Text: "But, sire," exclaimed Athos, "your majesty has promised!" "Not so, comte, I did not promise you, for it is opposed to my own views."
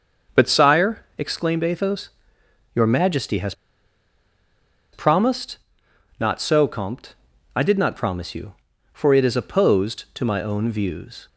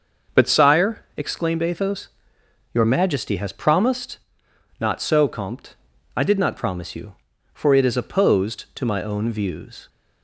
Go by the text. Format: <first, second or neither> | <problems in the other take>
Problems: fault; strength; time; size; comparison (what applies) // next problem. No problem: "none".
second | starts louder than the rest; until 1.4 s; 6 dB; also in the second // pauses between "has" and "promised"; strong; at 3.5 s; 1.4 s long